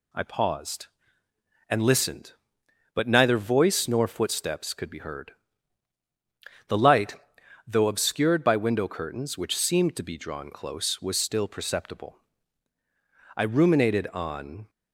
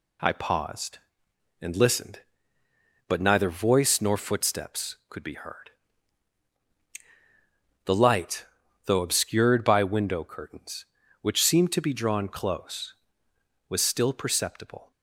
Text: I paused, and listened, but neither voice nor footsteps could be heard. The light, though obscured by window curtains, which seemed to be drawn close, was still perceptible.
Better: second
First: goes on to say "I ruminated on"; from 13.3 s on; 1.3 s long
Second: none

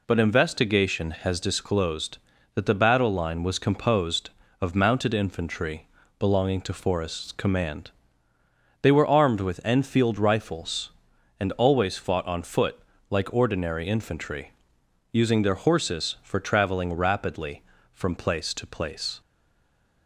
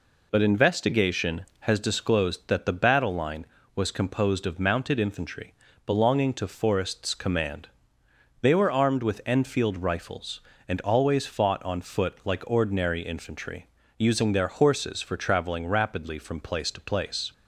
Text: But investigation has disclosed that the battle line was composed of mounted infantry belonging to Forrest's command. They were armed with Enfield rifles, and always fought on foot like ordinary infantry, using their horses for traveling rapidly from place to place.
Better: second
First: pauses between "infantry" and "belonging"; slight; at 5.8 s; 0.30 s long // pauses between "foot" and "like"; slight; at 12.7 s; 0.30 s long // stays silent after the last word; slight; from 19.2 s on; 0.8 s long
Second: pauses between "infantry" and "belonging"; slight; at 5.5 s; 0.34 s long

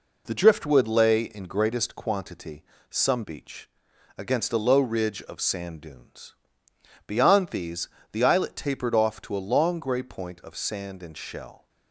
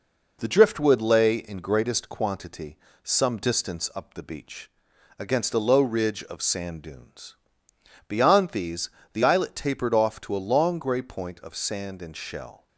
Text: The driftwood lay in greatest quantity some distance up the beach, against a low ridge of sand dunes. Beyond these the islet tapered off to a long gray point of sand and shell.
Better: second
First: pauses between "quantity" and "some"; slight; at 2.6 s; 0.26 s long // skips "distance up the"; at 3.2 s // pauses between "these" and "the"; slight; at 7.8 s; 0.24 s long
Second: pauses between "quantity" and "some"; slight; at 2.7 s; 0.26 s long // pauses between "these" and "the"; slight; at 8.8 s; 0.24 s long

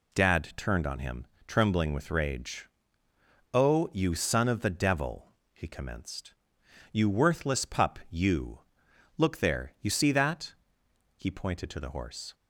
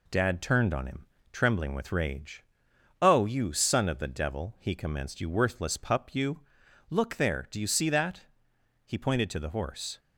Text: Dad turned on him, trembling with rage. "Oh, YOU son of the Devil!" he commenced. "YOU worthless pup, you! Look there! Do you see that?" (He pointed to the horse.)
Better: second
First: skips "Do"; at 9.7 s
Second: none

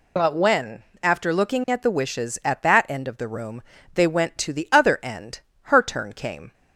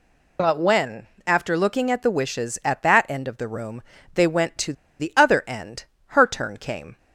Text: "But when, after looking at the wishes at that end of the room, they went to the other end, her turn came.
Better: first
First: none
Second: pauses between "to" and "the"; slight; at 4.7 s; 0.27 s long

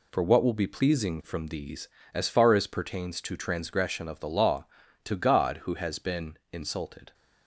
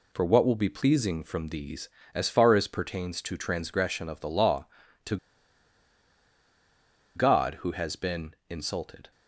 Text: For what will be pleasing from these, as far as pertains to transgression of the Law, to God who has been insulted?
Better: first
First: none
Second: pauses between "to" and "God"; strong; at 5.1 s; 1.9 s long

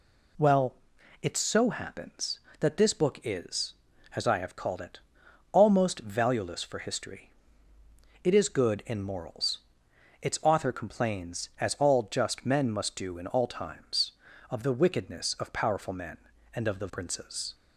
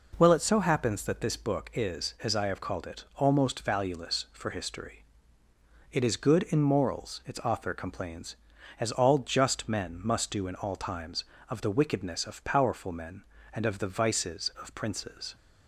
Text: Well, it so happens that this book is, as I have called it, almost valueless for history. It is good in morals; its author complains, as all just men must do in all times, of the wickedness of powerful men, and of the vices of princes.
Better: second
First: skips "vices of"; at 16.9 s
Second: none

